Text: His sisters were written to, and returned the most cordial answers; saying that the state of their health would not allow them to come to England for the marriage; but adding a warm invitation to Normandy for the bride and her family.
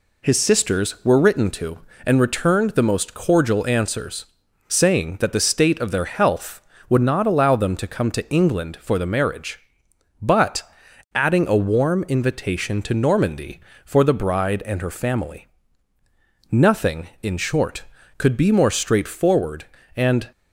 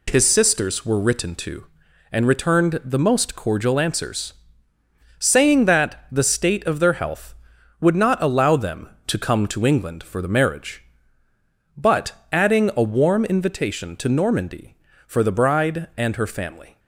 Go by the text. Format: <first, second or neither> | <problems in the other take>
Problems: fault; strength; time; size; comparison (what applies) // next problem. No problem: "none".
second | pauses between "but" and "adding"; noticeable; at 10.6 s; 0.52 s long; slight in the second // goes on to say "Nothing in short could be more straightforward and"; strong; from 16.4 s on; 3.8 s long